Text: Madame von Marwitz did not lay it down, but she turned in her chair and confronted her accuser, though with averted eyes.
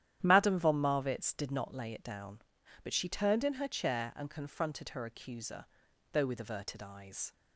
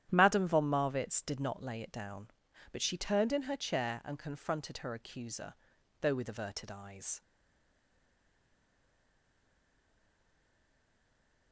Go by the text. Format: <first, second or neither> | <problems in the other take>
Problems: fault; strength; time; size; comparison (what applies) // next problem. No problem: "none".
first | starts louder than the rest; strong; until 1.1 s; 11 dB; strong in the first // stays silent after the last word; strong; from 7.2 s on; 4.3 s long